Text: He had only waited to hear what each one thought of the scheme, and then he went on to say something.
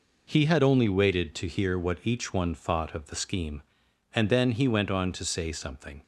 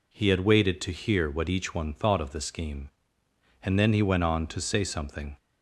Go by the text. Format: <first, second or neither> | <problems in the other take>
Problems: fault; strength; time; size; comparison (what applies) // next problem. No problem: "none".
first | skips "only"; at 0.4 s